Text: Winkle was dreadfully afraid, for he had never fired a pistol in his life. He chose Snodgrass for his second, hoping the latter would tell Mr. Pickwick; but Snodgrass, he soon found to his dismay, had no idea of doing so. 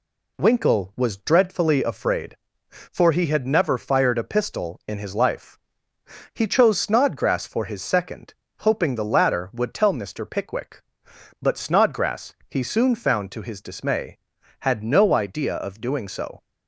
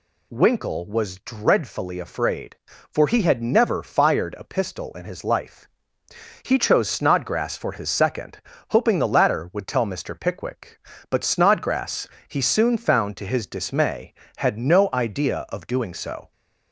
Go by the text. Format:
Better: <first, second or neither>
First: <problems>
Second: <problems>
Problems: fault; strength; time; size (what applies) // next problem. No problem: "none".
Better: neither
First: none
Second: none